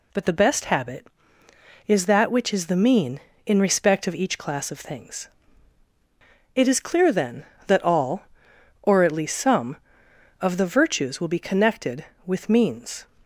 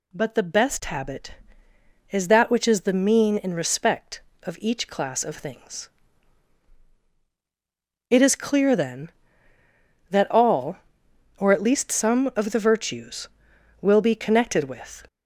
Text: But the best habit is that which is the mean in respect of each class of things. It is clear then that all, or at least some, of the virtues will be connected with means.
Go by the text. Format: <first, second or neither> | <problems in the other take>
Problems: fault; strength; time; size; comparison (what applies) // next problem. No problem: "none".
first | stops before "means"; at 15.0 s